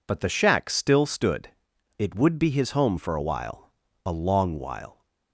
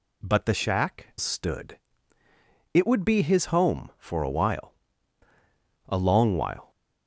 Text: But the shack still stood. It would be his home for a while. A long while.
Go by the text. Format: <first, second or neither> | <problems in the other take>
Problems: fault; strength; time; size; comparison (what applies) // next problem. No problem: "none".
first | skips "still"; at 1.1 s